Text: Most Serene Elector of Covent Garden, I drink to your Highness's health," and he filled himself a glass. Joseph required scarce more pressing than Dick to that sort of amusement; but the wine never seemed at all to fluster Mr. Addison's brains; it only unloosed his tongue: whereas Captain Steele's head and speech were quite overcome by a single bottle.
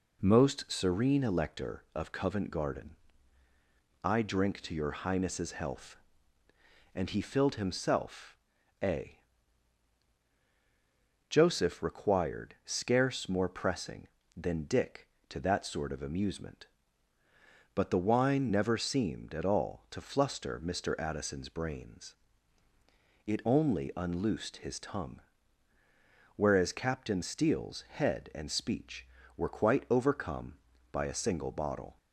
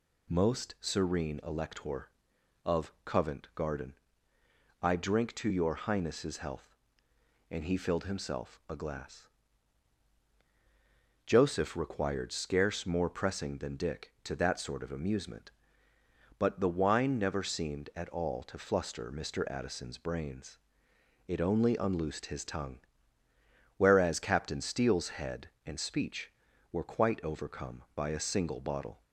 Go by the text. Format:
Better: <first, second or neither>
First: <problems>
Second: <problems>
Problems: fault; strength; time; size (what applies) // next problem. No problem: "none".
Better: second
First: pauses between "himself" and "a"; noticeable; at 8.3 s; 0.46 s long // skips "glass"; at 10.2 s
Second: none